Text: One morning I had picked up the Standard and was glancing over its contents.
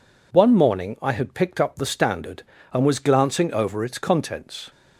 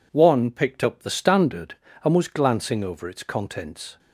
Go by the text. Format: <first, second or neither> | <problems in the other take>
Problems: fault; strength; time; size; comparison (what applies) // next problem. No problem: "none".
first | skips "morning I had"; at 0.4 s